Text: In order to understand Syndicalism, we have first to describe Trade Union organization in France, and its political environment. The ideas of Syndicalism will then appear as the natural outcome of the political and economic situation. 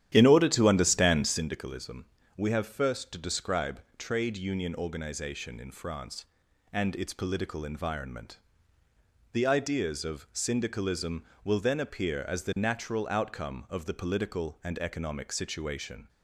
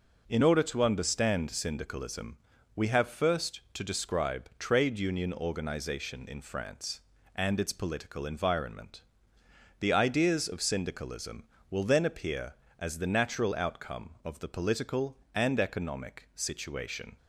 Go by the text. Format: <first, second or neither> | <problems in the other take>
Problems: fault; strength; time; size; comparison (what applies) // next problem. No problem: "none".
second | starts louder than the rest; strong; until 1.5 s; 11 dB // pauses between "describe" and "Trade"; slight; at 3.8 s; 0.16 s long